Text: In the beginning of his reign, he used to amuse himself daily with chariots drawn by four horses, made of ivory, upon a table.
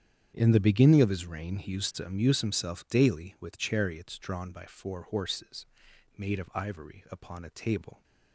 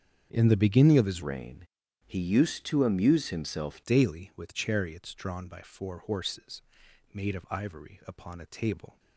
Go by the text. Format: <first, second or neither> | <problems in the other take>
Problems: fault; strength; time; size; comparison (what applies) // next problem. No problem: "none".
first | starts louder than the rest; strong; until 1.3 s; 7.5 dB; strong in the first // changes voice from "reign" to "himself"; from 1.2 to 3.8 s; 2.6 s long